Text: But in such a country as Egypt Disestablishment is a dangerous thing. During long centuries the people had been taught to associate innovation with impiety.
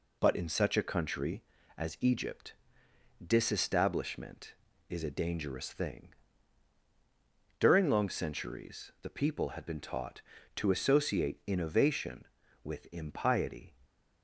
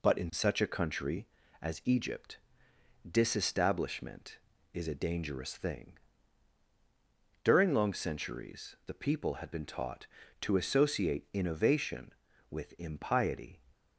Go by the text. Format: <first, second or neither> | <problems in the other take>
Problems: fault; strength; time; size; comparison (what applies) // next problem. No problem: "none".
neither | pauses between "Egypt" and "Disestablishment"; noticeable; the same in both